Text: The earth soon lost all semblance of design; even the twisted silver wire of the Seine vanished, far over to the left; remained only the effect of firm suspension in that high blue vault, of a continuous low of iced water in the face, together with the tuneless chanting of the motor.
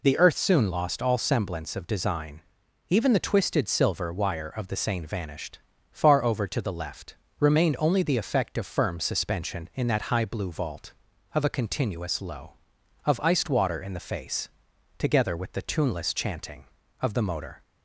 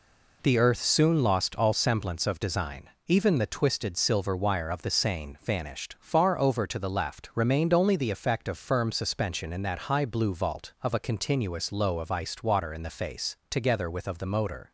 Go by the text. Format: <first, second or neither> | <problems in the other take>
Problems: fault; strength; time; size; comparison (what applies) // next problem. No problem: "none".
first | skips "the tuneless chanting"; at 14.0 s